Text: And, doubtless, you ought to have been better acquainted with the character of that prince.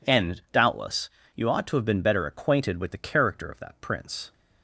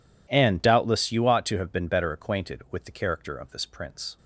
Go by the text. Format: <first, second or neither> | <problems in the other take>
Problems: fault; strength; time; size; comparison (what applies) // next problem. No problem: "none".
first | says "this" for "that"; at 3.5 s